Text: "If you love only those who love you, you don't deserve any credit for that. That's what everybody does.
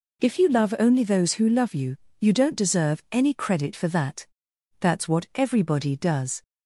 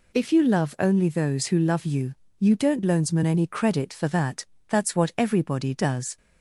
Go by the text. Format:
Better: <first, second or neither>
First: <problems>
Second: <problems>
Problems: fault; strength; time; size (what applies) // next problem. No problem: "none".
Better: first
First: none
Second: says "loansman" for "deserve"; at 2.8 s